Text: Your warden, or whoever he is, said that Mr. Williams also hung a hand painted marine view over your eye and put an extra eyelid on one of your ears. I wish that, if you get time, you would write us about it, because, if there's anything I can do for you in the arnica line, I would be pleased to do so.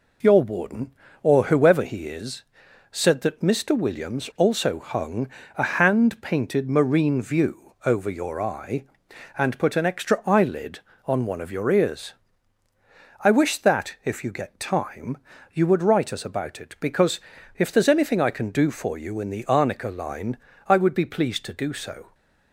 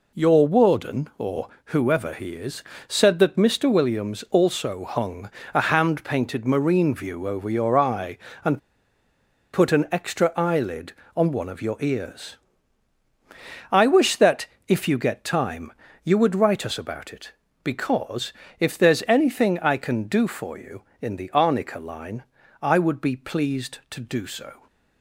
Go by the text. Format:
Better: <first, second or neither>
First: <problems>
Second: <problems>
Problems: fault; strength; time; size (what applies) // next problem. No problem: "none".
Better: first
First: pauses between "hung" and "a"; slight; at 5.2 s; 0.28 s long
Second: pauses between "or" and "whoever"; slight; at 1.4 s; 0.16 s long // pauses between "hung" and "a"; slight; at 5.3 s; 0.24 s long // pauses between "and" and "put"; noticeable; at 8.5 s; 0.94 s long